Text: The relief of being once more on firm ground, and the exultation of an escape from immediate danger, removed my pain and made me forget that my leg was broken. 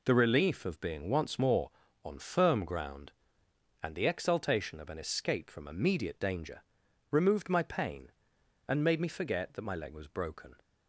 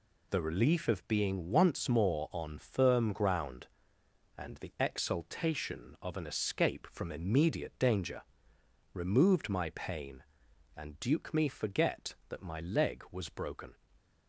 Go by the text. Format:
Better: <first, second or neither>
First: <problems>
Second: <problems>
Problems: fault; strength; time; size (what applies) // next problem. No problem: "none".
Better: first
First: none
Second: says "duke" for "made"; at 10.9 s